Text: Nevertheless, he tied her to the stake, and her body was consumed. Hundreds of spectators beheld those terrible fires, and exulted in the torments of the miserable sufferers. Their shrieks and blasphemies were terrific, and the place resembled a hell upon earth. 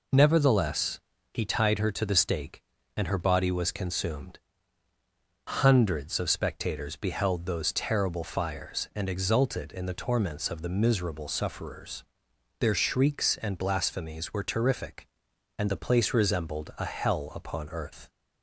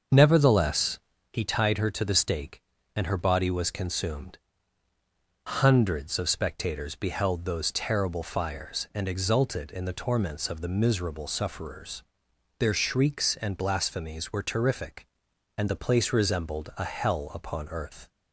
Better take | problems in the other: first | starts louder than the rest; until 1.2 s; 6.5 dB

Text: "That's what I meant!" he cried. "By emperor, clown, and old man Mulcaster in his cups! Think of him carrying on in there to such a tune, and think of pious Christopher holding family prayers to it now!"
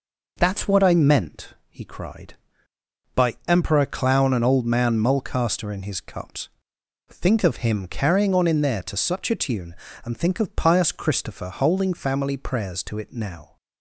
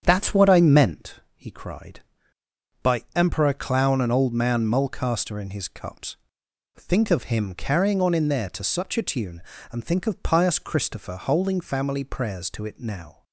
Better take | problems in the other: first | starts louder than the rest; strong; until 1.0 s; 8 dB

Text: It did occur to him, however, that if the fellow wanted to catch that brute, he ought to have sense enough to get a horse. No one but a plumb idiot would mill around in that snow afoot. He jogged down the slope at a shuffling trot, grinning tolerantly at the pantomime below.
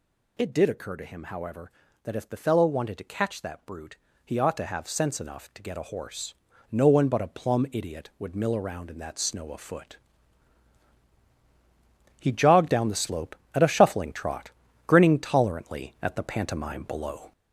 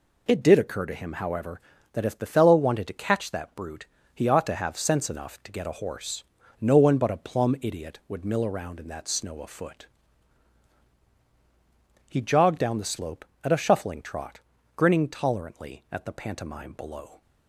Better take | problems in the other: second | gets louder; noticeable; throughout; 4.5 dB

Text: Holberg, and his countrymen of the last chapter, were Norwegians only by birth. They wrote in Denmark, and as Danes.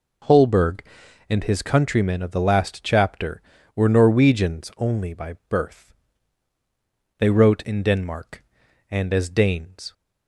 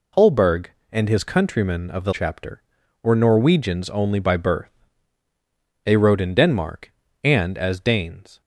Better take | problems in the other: first | skips "last"; at 2.1 s

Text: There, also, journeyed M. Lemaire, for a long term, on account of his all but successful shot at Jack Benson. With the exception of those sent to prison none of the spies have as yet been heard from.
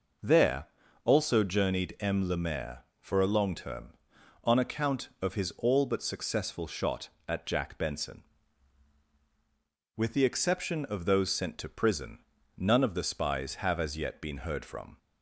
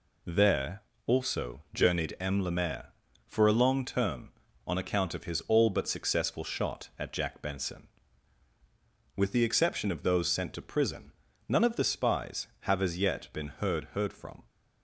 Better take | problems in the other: first | pauses between "prison" and "none"; slight; at 11.1 s; 0.36 s long; also in the first // says "heard" twice; at 13.9 s

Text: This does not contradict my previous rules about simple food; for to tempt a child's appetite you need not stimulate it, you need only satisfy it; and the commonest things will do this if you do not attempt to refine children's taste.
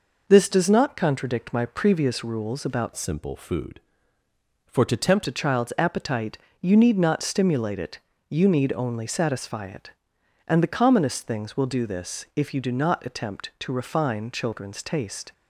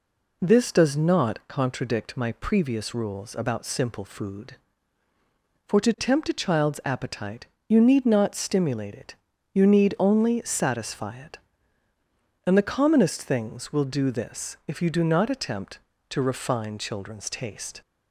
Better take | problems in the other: second | changes voice from "simple" to "tempt"; from 2.9 to 5.2 s; 2.3 s long // pauses between "appetite" and "you"; slight; at 6.3 s; 0.22 s long; slight in the second

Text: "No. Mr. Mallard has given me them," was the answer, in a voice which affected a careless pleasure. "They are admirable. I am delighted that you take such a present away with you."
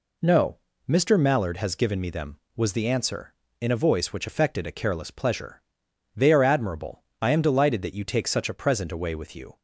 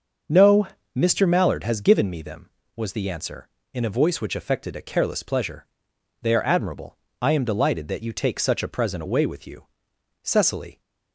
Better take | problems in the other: first | starts louder than the rest; until 1.5 s; 6.5 dB // goes on to say "Cecily"; from 10.2 s on; 0.56 s long

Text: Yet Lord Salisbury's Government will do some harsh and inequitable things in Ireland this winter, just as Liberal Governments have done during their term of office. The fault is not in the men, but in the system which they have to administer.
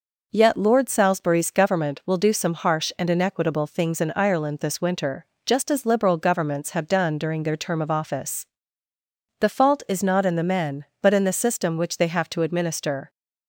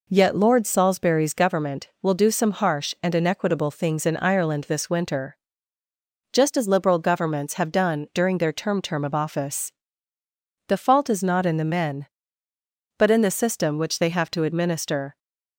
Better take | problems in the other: first | says "term" twice; at 8.8 s

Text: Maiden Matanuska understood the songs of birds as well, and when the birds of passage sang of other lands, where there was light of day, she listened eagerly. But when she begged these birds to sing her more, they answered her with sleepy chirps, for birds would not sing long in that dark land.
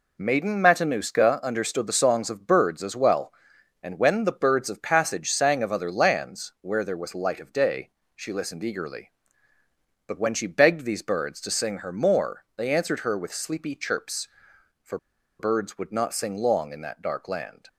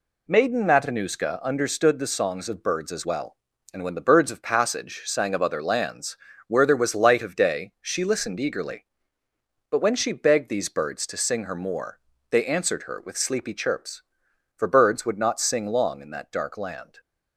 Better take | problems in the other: second | pauses between "for" and "birds"; at 14.9 s; 0.41 s long

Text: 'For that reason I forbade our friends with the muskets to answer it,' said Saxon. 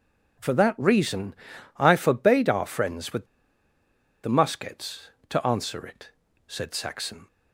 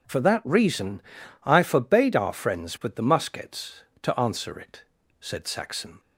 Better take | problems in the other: second | pauses between "reason" and "I"; at 1.3 s; 0.44 s long; also in the second // pauses between "with" and "the"; noticeable; at 3.2 s; 0.97 s long

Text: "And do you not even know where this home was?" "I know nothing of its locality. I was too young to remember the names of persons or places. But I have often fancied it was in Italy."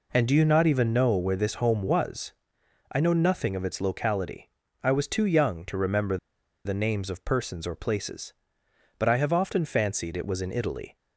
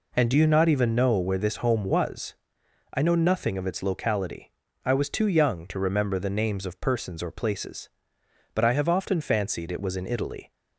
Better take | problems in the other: second | pauses between "remember" and "the"; noticeable; at 6.1 s; 0.48 s long

